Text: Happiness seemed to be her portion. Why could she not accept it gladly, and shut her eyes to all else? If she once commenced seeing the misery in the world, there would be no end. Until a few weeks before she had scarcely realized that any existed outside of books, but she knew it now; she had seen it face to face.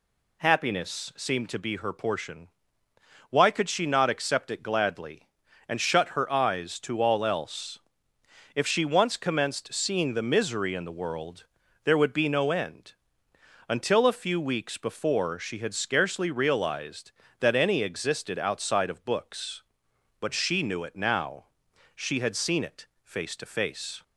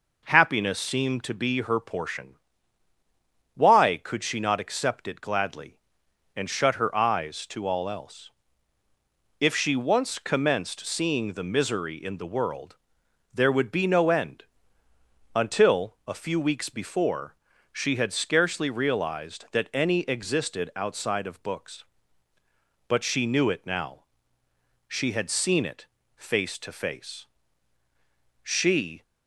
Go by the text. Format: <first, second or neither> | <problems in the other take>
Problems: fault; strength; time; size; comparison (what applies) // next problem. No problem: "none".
first | pauses between "before" and "she"; at 17.3 s; 0.38 s long // pauses between "it" and "face"; slight; at 25.8 s; 0.30 s long; slight in the first // goes on to say "She"; noticeable; from 28.4 s on; 0.62 s long